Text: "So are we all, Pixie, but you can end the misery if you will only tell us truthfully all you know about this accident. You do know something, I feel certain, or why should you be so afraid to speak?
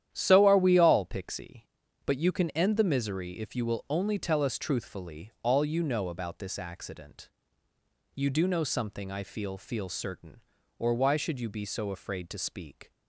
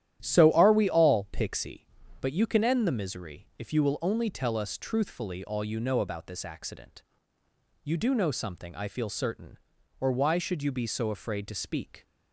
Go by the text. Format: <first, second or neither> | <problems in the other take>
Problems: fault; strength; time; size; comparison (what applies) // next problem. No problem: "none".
second | starts louder than the rest; strong; until 1.1 s; 10.5 dB; strong in the second // says "feel" twice; at 9.5 s